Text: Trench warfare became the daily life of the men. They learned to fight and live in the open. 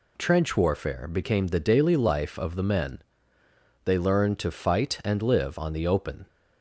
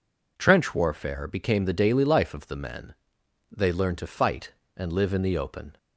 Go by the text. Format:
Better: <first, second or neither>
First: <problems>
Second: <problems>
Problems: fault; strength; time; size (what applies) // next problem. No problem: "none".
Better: second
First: says "on" for "in"; at 5.5 s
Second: none